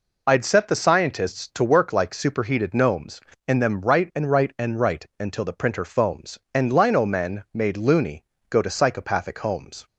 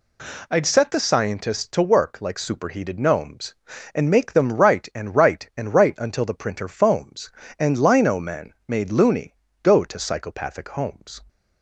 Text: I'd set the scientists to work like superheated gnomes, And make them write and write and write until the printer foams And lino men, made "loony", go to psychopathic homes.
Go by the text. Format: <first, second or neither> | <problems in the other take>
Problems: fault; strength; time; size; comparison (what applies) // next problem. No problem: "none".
second | skips "make"; at 3.6 s